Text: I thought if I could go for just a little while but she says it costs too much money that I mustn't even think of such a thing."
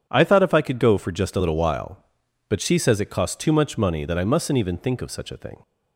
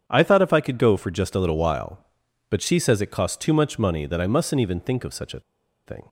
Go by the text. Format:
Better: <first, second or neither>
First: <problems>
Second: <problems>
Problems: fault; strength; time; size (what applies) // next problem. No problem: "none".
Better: first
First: starts louder than the rest; strong; until 1.1 s; 9 dB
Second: starts louder than the rest; strong; until 1.0 s; 8.5 dB // pauses between "a" and "thing"; at 5.4 s; 0.45 s long